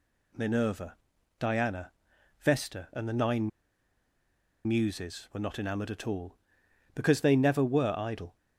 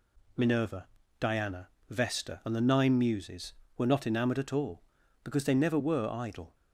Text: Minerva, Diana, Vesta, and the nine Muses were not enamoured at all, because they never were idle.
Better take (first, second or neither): second